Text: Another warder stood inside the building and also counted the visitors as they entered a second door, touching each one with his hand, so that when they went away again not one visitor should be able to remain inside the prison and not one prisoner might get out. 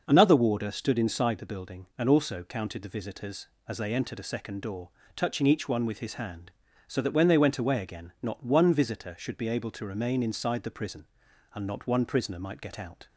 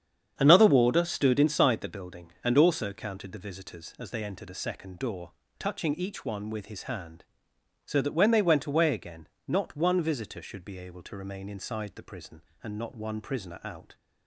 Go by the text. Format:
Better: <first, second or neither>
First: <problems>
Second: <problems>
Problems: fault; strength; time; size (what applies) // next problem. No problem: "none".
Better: first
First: starts louder than the rest; noticeable; until 1.0 s; 6 dB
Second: starts louder than the rest; strong; until 1.3 s; 8 dB // pauses between "again" and "not"; slight; at 9.2 s; 0.20 s long // skips "might get"; at 13.6 s